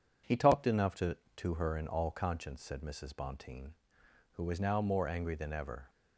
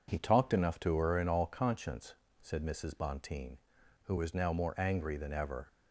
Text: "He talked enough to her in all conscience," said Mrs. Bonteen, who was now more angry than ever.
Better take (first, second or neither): second